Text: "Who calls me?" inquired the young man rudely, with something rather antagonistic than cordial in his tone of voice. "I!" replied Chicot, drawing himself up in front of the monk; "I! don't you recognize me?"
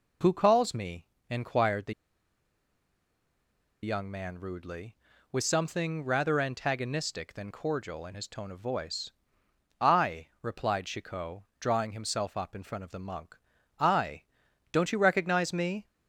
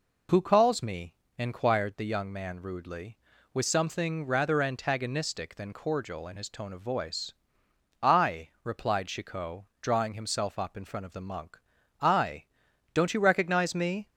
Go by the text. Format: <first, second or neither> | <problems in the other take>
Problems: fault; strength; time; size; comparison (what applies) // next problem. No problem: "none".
second | pauses between "the" and "young"; strong; at 1.9 s; 1.9 s long